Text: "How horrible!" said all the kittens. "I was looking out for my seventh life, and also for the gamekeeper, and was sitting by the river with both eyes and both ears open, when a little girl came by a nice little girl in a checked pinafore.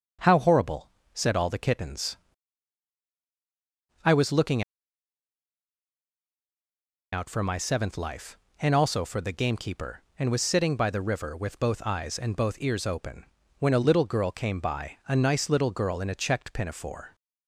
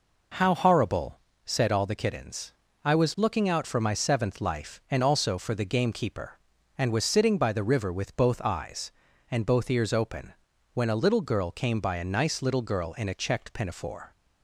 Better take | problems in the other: second | starts louder than the rest; until 1.4 s; 7 dB // pauses between "looking" and "out"; strong; at 4.6 s; 2.5 s long

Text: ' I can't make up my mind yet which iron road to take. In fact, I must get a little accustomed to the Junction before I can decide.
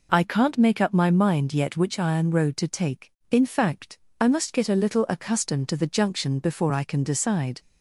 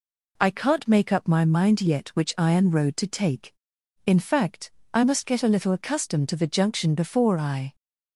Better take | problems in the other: first | stops before "can decide"; at 7.7 s

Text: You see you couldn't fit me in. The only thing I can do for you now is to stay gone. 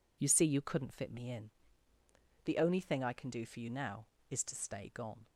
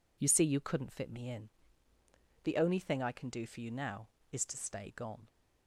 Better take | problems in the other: neither | none

